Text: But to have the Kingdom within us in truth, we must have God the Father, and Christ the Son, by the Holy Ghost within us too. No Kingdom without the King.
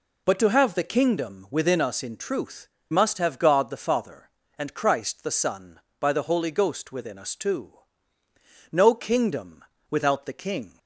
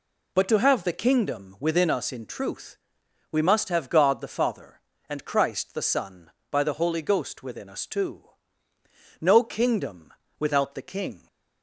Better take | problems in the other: second | skips "we"; at 2.7 s // pauses between "Kingdom" and "without"; slight; at 9.6 s; 0.26 s long; slight in the second

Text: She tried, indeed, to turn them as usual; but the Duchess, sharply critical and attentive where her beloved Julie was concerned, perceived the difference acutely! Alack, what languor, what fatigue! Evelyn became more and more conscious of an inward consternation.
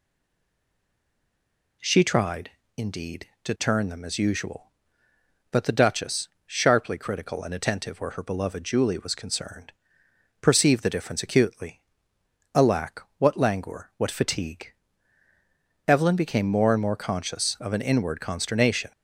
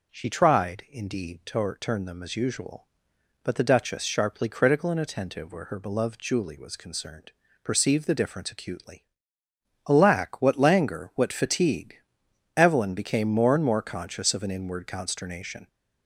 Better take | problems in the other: second | stays silent before the first word; noticeable; until 1.7 s; 1.7 s long

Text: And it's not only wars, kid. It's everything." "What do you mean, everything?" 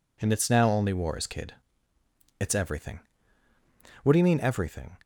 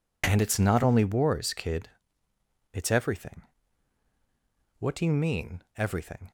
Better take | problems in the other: second | says "now" for "not"; at 0.4 s

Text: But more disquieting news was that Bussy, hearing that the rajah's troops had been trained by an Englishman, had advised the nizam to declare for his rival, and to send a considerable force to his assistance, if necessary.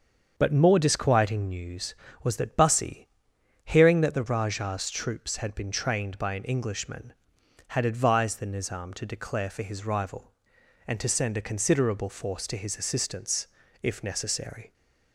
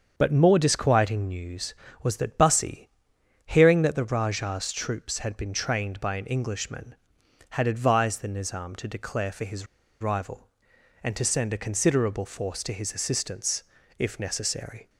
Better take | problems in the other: first | starts louder than the rest; until 1.1 s; 7 dB; also in the first // pauses between "his" and "rival"; slight; at 9.6 s; 0.34 s long

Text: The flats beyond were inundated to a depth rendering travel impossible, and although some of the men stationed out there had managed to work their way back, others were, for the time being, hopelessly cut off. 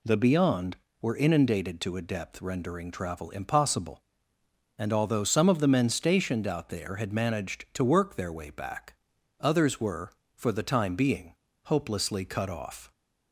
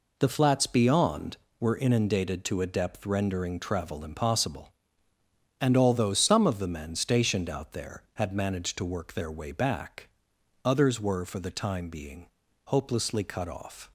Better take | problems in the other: second | skips "flats"; at 0.1 s

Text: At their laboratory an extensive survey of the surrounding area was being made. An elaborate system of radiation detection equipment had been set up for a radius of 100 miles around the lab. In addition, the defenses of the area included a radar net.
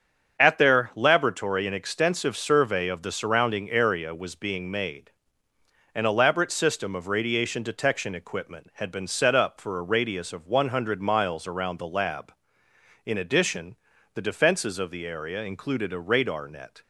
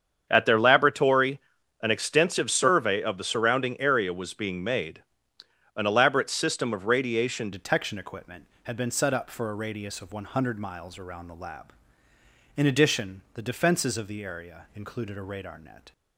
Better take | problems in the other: first | starts louder than the rest; strong; until 1.3 s; 7.5 dB; strong in the first // pauses between "laboratory" and "an"; at 1.3 s; 0.42 s long // changes voice at "detection"; from 7.5 s on; 8.4 s long

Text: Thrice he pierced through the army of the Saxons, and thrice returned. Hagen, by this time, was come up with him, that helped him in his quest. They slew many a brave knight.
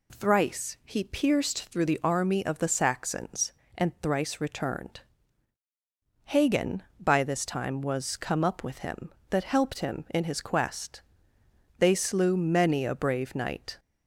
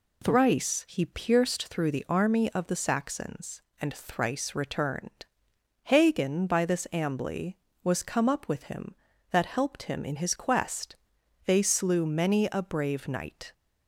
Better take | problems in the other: first | says "ambly" for "time"; at 6.9 s

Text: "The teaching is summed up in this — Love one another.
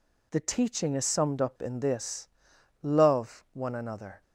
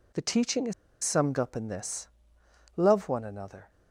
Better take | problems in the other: first | pauses between "is" and "summed"; slight; at 0.7 s; 0.30 s long

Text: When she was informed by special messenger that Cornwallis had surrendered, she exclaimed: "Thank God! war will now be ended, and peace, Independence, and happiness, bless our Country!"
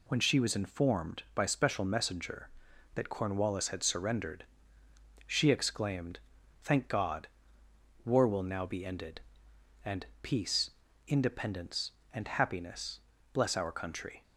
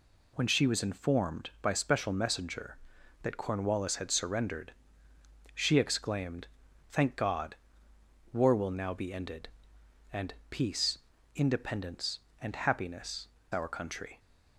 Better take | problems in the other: first | pauses between "and" and "peace"; slight; at 10.3 s; 0.16 s long; slight in the first // skips "bless"; at 13.4 s

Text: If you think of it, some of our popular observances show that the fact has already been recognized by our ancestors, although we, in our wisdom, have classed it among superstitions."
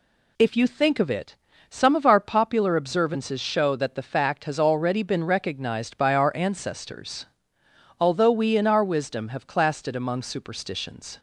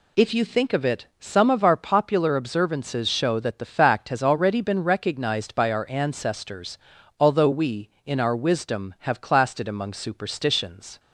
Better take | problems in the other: neither | none

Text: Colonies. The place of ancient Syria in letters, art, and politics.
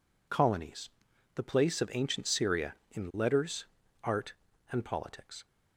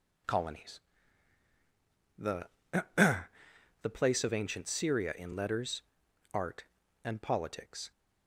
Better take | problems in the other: first | says "The" twice; at 2.9 s

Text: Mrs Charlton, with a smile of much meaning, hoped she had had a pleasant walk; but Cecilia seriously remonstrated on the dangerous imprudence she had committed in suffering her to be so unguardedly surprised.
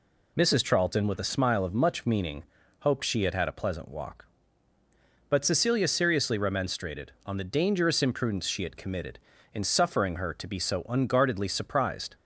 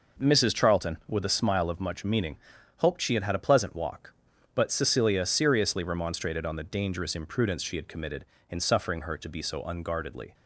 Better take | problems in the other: first | stops before "surprised"; at 10.3 s

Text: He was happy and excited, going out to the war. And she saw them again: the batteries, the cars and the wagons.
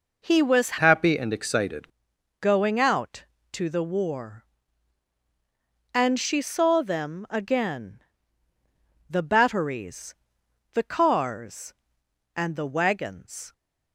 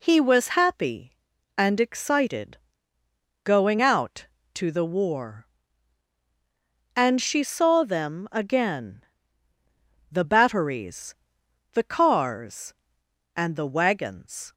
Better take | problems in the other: second | changes voice from "happy" to "excited"; from 0.7 to 1.8 s; 1.1 s long

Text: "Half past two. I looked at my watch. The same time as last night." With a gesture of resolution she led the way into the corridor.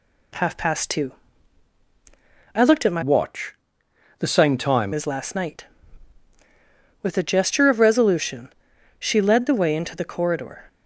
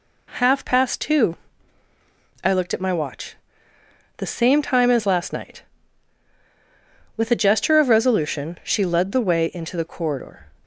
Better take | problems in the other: second | changes voice from "watch" to "time"; from 3.0 to 4.9 s; 1.9 s long // pauses between "resolution" and "she"; noticeable; at 8.5 s; 0.48 s long

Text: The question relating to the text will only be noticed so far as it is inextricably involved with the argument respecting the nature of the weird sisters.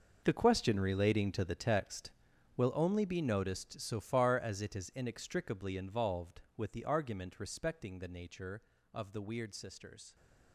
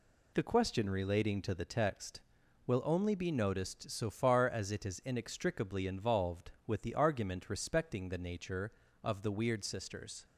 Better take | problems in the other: second | gets quieter; strong; throughout; 14.5 dB

